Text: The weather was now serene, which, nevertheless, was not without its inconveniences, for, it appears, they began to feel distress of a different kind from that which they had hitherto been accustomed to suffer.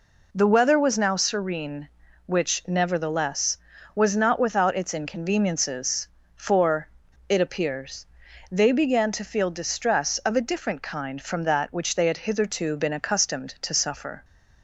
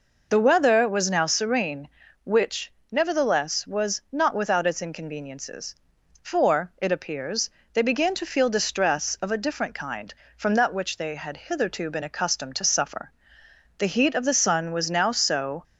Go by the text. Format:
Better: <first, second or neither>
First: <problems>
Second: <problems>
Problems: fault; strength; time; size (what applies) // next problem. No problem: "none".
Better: first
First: none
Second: goes on to say "The heat of the sun was now so"; strong; from 13.7 s on; 1.8 s long